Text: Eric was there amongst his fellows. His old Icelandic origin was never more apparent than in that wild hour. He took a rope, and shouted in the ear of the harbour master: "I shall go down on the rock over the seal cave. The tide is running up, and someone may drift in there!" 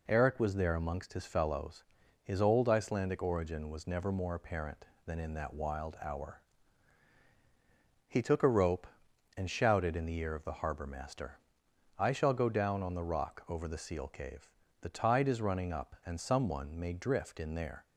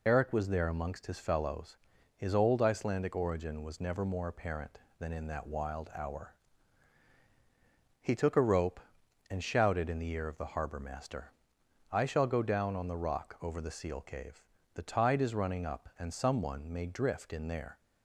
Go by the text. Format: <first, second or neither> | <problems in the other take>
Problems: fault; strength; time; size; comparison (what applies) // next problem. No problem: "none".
first | loses the start of "Eric"; at 0.0 s; 50 ms